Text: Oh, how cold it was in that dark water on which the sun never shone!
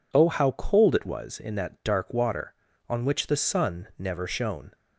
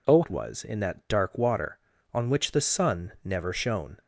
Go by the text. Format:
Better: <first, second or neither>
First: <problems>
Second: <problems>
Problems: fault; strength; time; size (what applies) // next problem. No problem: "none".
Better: first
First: none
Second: skips "how cold"; at 0.2 s